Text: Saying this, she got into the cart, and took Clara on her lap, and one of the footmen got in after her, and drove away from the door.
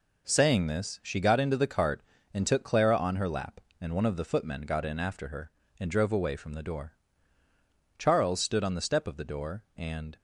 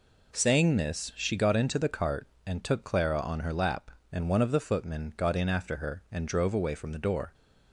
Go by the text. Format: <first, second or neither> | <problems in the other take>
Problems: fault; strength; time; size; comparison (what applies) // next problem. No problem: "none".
second | goes on to say "Charles stood on the step of the door and"; strong; from 7.9 s on; 2.1 s long